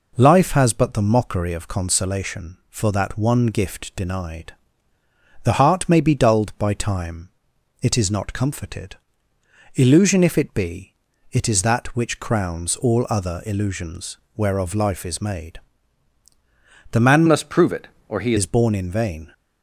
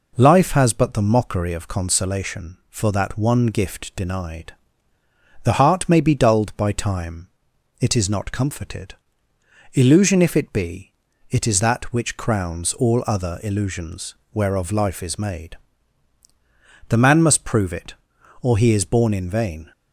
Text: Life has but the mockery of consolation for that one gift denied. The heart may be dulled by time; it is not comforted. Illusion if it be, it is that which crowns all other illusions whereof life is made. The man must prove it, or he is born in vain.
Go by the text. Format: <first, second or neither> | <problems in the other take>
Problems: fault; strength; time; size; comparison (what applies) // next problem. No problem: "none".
second | pauses between "illusions" and "whereof"; slight; at 14.1 s; 0.18 s long; slight in the second // changes voice from "must" to "he"; from 17.2 to 18.3 s; 1.1 s long